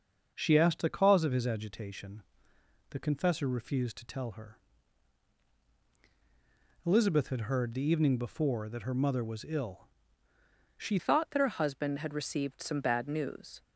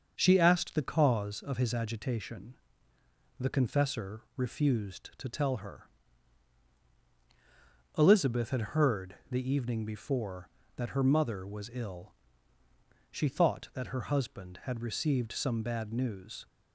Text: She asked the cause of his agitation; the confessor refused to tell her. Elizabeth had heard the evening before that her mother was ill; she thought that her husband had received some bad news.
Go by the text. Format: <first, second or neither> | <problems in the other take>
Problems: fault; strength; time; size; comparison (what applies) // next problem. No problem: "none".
second | starts louder than the rest; until 1.3 s; 6.5 dB; also in the second // changes voice at "thought"; from 10.9 s on; 2.7 s long